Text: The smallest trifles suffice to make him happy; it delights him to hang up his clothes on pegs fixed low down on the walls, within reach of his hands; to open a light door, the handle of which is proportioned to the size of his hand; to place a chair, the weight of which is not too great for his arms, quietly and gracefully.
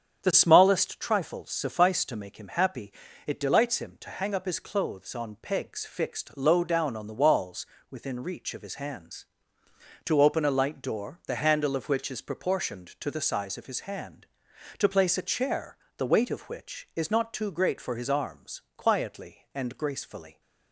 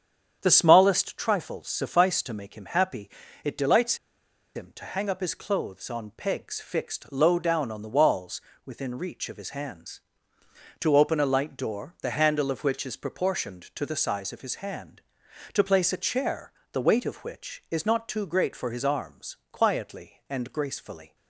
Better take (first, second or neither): first